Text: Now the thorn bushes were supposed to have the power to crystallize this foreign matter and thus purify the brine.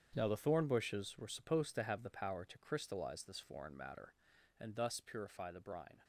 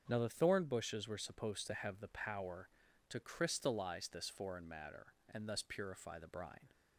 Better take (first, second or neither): second